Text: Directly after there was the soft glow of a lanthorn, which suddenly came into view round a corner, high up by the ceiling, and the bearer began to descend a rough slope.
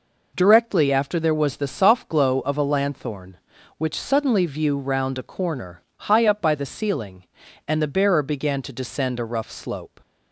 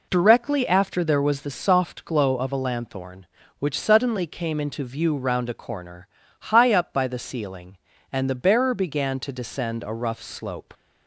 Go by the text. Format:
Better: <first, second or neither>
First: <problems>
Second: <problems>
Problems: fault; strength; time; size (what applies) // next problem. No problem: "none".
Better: second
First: skips "came into"; at 4.4 s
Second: none